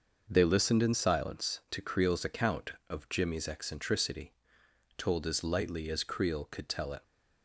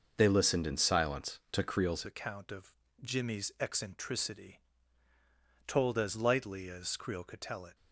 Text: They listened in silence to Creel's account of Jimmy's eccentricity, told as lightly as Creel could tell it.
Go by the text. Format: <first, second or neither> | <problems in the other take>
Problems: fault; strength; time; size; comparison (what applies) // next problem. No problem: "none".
first | starts louder than the rest; noticeable; until 1.1 s; 6 dB; also in the first // changes voice at "account"; from 2.0 s on; 5.7 s long // pauses between "of" and "Jimmy's"; slight; at 2.7 s; 0.28 s long